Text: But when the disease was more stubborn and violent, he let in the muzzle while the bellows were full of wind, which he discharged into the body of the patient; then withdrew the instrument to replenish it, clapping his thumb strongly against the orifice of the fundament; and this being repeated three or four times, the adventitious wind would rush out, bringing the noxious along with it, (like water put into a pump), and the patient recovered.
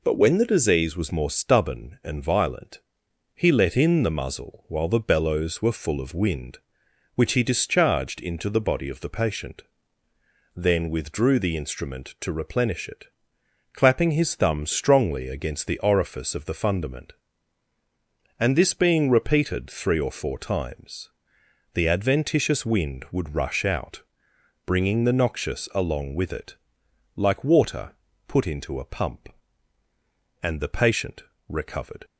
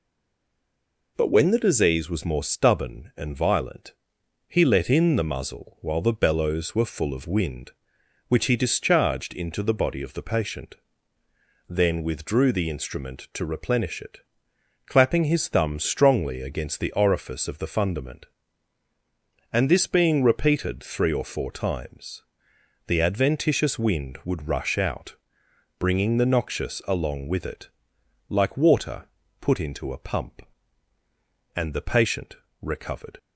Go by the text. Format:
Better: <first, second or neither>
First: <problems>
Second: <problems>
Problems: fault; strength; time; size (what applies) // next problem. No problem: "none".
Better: first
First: pauses between "water" and "put"; slight; at 27.9 s; 0.34 s long // pauses between "patient" and "recovered"; slight; at 31.2 s; 0.26 s long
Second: stays silent before the first word; noticeable; until 1.1 s; 1.1 s long // pauses between "water" and "put"; slight; at 29.0 s; 0.34 s long // pauses between "patient" and "recovered"; slight; at 32.3 s; 0.26 s long